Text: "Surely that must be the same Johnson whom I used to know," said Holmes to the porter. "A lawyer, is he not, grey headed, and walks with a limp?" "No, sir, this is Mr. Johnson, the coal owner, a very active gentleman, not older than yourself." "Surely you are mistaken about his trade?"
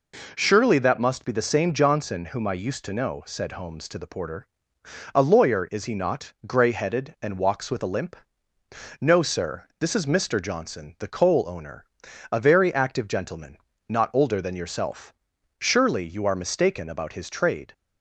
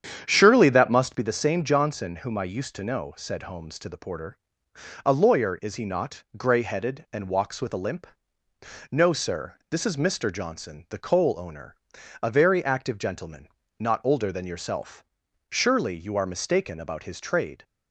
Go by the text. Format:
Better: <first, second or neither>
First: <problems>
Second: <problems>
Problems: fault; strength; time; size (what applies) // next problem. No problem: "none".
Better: first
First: none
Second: starts louder than the rest; strong; until 1.3 s; 8.5 dB